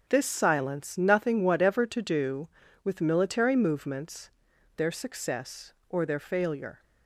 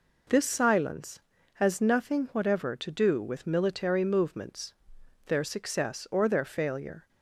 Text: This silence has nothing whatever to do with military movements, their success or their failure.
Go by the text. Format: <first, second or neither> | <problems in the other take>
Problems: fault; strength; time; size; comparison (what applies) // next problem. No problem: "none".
second | skips "has"; at 0.9 s